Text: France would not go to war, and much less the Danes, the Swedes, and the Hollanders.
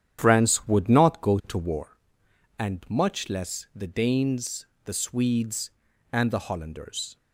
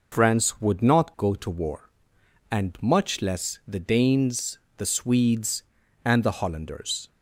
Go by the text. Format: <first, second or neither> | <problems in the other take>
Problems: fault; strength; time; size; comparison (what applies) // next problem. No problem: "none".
second | starts louder than the rest; strong; until 1.9 s; 9.5 dB